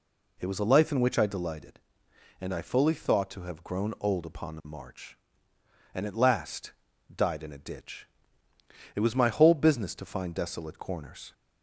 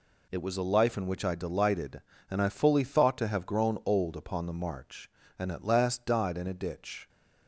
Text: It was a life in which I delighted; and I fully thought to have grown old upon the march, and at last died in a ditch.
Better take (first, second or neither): second